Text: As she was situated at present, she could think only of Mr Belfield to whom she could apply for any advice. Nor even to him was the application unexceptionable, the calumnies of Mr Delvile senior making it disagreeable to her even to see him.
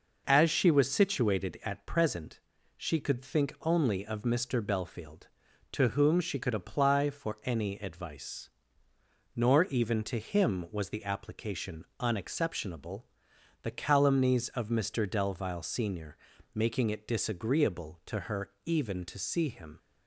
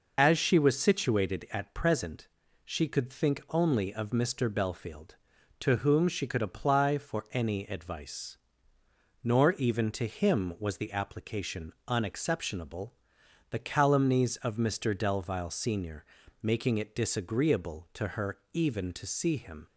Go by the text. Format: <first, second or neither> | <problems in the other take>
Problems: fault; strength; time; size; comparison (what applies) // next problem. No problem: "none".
first | loses the start of "As"; at 0.1 s; 35 ms // pauses between "application" and "unexceptionable"; slight; at 11.7 s; 0.16 s long; slight in the first // pauses between "senior" and "making"; at 16.0 s; 0.42 s long; also in the first